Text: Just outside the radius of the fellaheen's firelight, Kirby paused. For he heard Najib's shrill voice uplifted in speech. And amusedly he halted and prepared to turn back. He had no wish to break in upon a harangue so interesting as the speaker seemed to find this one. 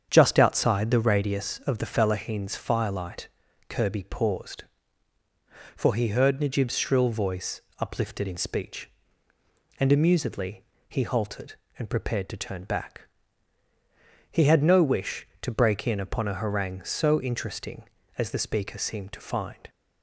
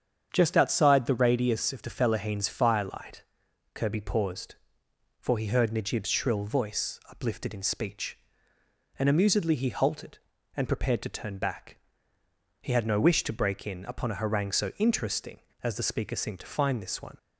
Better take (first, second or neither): second